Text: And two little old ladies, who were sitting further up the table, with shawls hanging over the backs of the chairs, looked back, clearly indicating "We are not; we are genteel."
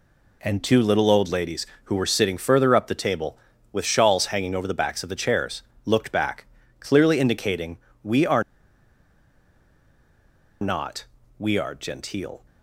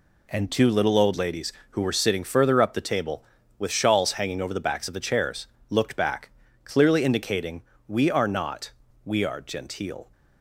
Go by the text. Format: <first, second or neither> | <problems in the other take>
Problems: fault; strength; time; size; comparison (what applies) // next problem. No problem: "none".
second | pauses between "indicating" and "We"; slight; at 7.7 s; 0.26 s long; slight in the second // pauses between "are" and "not"; strong; at 8.4 s; 2.1 s long